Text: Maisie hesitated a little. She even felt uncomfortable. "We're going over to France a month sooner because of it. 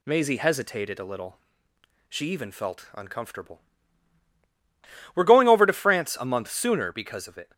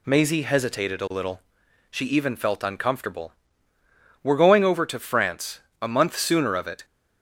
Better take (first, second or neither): first